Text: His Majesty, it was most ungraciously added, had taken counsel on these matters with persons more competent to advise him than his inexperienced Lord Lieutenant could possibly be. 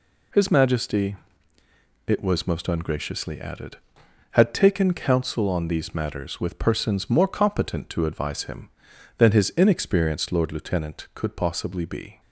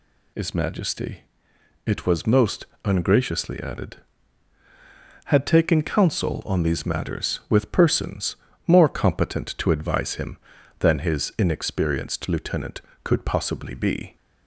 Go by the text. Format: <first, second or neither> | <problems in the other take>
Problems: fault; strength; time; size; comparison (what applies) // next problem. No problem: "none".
first | pauses between "most" and "ungraciously"; slight; at 2.6 s; 0.18 s long // pauses between "persons" and "more"; slight; at 8.3 s; 0.32 s long // skips "Lord"; at 12.2 s